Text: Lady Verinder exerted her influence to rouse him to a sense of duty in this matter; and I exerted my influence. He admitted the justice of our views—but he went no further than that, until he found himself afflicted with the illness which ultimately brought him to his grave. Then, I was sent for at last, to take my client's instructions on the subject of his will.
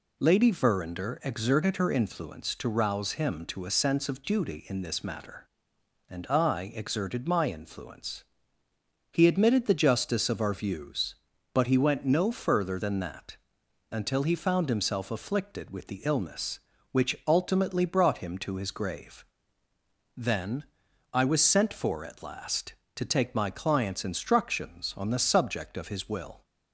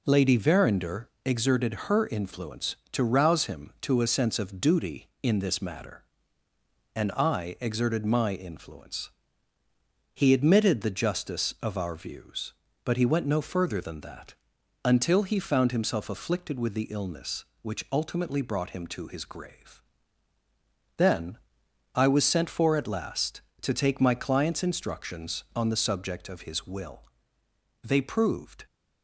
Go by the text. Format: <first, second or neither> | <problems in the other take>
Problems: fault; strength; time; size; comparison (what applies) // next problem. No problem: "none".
first | pauses between "Verinder" and "exerted"; slight; at 1.0 s; 0.16 s long // goes on to say "They proved"; noticeable; from 27.8 s on; 0.82 s long